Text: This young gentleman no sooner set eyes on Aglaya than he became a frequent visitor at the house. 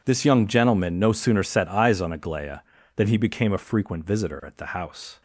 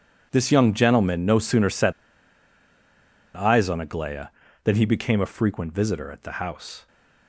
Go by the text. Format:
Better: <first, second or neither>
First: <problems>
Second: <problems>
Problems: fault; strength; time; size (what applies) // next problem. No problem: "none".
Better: first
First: none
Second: pauses between "set" and "eyes"; strong; at 1.9 s; 1.4 s long